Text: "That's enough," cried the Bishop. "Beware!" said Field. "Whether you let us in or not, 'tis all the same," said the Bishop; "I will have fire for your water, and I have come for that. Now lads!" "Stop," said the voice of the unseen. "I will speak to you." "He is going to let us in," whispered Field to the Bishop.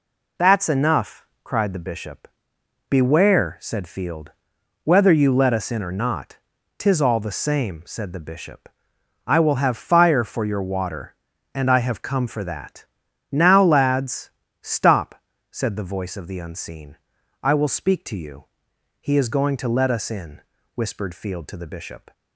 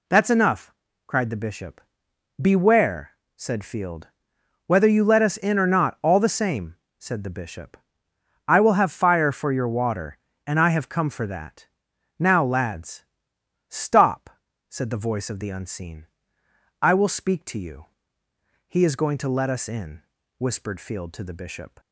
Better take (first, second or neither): first